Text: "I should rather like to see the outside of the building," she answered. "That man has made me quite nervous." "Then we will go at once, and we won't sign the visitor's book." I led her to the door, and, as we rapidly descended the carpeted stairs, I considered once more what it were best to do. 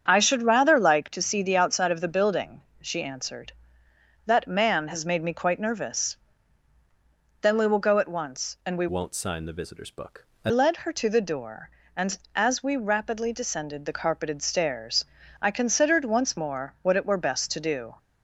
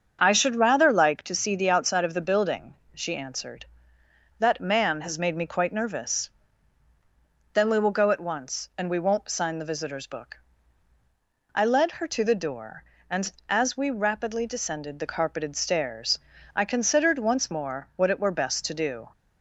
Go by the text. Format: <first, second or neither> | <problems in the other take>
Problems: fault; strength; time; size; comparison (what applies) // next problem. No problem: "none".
second | starts louder than the rest; strong; until 1.0 s; 7.5 dB; also in the second // changes voice from "won't" to "I"; from 8.8 to 10.4 s; 1.6 s long